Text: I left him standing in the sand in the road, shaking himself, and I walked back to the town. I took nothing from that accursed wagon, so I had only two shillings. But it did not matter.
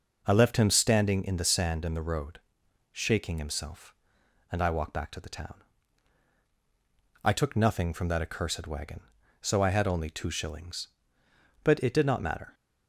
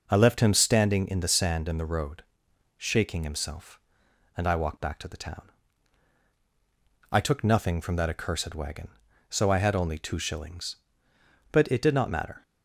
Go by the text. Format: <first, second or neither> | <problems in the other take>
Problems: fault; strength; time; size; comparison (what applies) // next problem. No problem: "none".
neither | none